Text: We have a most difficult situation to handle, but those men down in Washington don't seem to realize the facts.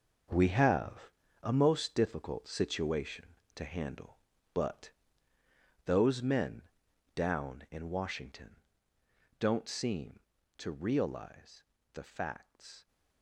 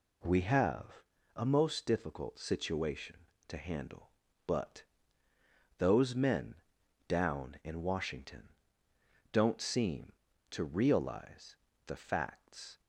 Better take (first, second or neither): second